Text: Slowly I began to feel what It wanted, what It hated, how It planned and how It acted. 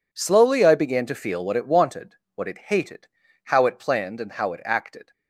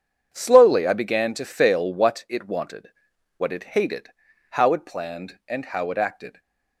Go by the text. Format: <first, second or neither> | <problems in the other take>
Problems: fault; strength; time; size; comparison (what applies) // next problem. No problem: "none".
first | starts louder than the rest; strong; until 1.3 s; 8 dB // says "fail" for "feel"; at 1.4 s // stays silent after the last word; slight; from 6.3 s on; 0.5 s long